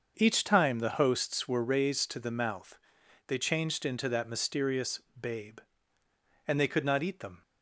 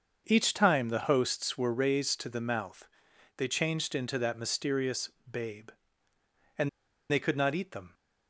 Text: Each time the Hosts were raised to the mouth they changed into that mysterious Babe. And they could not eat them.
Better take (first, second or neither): first